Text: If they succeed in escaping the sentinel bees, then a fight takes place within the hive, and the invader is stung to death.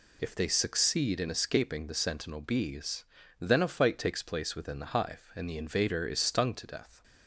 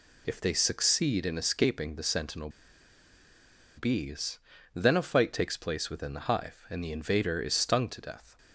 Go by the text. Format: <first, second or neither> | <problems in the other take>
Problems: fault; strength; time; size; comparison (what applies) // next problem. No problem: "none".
first | pauses between "sentinel" and "bees"; strong; at 2.4 s; 1.2 s long